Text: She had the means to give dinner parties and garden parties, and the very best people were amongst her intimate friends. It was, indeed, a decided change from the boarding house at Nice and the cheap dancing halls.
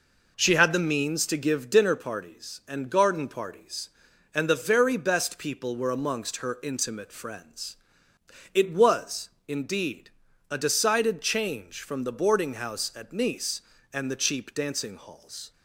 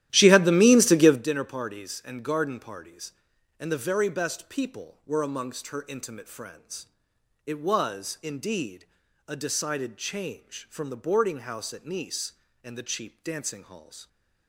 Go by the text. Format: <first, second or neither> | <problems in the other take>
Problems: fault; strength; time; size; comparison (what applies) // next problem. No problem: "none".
first | starts louder than the rest; strong; until 1.3 s; 13 dB